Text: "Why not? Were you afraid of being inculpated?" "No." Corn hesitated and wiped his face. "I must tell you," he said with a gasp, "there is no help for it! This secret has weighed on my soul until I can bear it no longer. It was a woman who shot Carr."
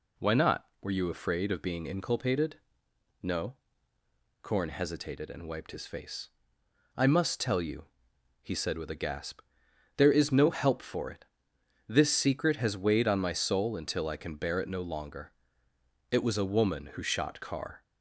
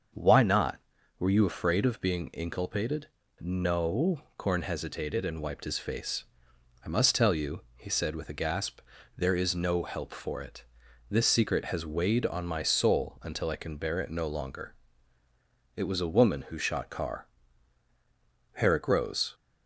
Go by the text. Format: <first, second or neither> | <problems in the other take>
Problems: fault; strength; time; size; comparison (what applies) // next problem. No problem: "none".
first | starts louder than the rest; until 1.5 s; 6.5 dB // goes on to say "Herrick rose"; noticeable; from 18.5 s on; 0.78 s long